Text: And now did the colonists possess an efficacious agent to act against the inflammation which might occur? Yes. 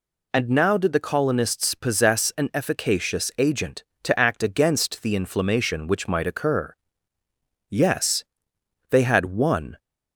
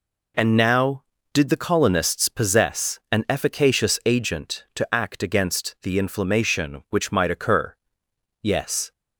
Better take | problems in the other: second | goes on to say "They had one"; noticeable; from 8.9 s on; 0.88 s long

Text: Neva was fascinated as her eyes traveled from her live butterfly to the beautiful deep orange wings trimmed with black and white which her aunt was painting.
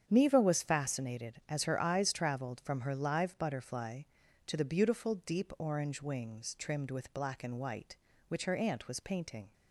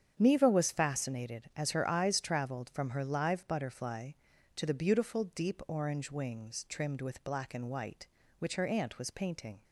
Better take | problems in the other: neither | starts louder than the rest; strong; the same in both

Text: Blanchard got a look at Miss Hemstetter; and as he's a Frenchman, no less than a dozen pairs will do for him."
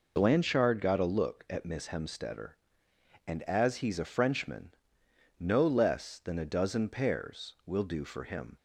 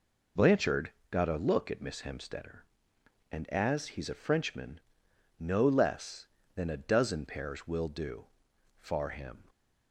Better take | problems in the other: first | pauses between "Blanchard" and "got"; slight; at 0.9 s; 0.18 s long // says "far" for "for"; at 8.8 s

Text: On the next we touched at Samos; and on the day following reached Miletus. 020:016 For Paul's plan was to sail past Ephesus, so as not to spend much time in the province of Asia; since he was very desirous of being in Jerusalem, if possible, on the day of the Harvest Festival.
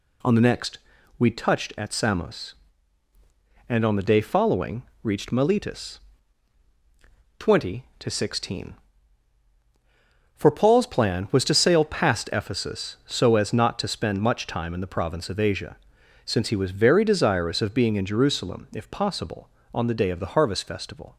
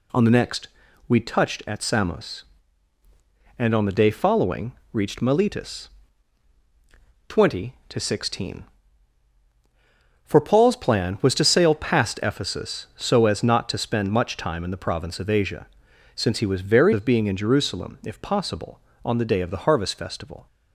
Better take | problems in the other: first | pauses between "next" and "we"; at 0.6 s; 0.40 s long; also in the first // pauses between "following" and "reached"; slight; at 4.7 s; 0.20 s long; slight in the first // skips "desirous"; at 16.9 s

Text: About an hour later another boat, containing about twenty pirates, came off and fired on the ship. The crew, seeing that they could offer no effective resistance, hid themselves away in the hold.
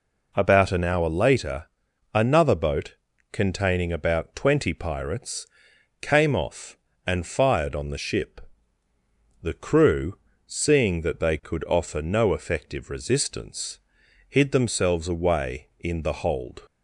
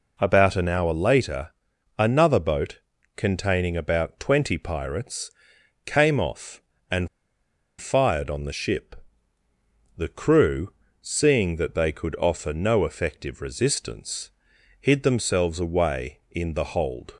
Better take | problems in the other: first | pauses between "later" and "another"; noticeable; at 1.5 s; 0.48 s long; noticeable in the first // pauses between "and" and "fired"; noticeable; at 7.0 s; 0.73 s long

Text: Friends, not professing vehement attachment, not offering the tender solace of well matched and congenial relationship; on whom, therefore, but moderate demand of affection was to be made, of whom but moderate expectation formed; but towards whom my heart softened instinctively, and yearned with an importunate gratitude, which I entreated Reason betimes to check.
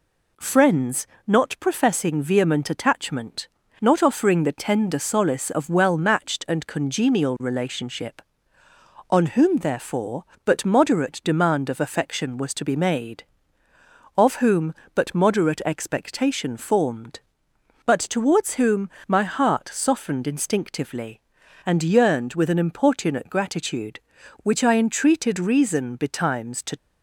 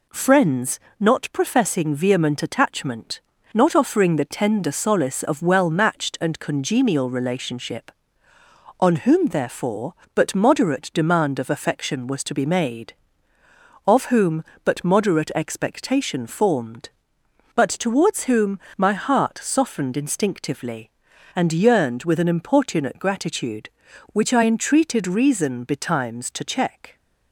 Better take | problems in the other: second | pauses between "whom" and "my"; slight; at 18.8 s; 0.20 s long; slight in the second // stops before "check"; at 26.7 s

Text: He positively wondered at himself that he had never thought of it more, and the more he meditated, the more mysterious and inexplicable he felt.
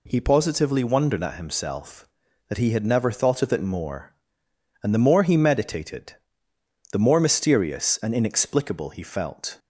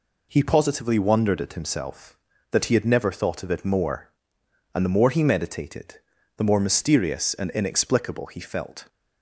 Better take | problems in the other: neither | none

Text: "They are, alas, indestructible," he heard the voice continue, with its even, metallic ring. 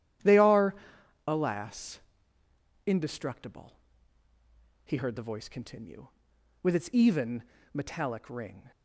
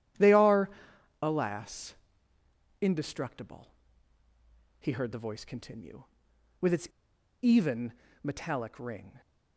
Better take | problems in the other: first | starts louder than the rest; strong; until 1.6 s; 10.5 dB; strong in the first // pauses between "its" and "even"; noticeable; at 6.8 s; 0.55 s long

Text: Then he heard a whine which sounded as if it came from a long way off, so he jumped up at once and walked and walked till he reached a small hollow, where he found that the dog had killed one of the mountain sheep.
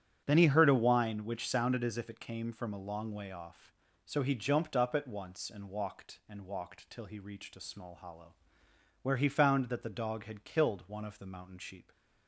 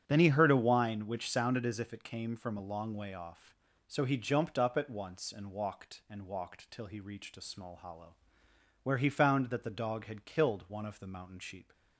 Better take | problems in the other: neither | starts louder than the rest; strong; the same in both

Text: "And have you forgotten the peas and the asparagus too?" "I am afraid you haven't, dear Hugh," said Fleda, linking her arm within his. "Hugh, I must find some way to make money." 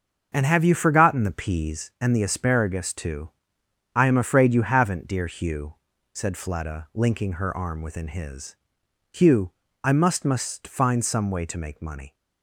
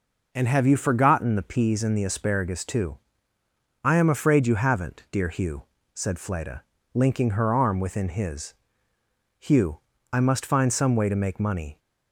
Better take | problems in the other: second | starts louder than the rest; until 1.3 s; 6.5 dB // says "must" twice; at 10.2 s

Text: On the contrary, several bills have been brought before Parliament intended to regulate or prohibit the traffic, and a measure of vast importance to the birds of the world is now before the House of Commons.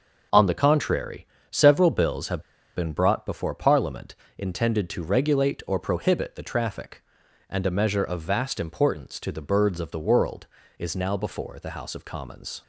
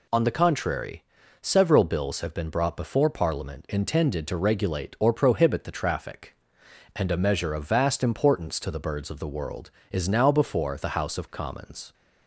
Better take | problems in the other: second | pauses between "have" and "been"; slight; at 2.3 s; 0.35 s long // pauses between "Parliament" and "intended"; slight; at 4.1 s; 0.24 s long

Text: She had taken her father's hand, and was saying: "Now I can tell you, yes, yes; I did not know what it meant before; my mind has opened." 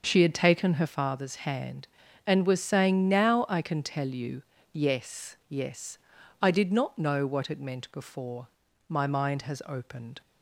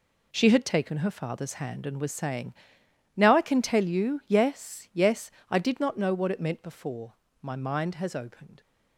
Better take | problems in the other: second | starts louder than the rest; until 1.1 s; 6.5 dB

